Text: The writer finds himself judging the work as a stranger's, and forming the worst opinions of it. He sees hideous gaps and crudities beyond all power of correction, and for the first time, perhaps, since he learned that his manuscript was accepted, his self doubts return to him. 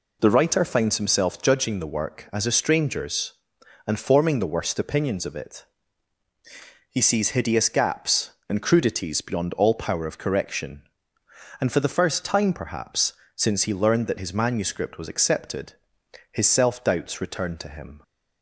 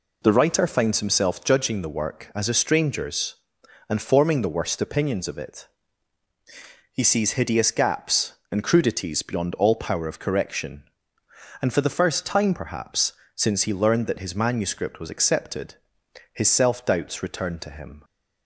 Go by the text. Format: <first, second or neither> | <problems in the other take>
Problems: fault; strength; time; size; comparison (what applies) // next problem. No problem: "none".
neither | none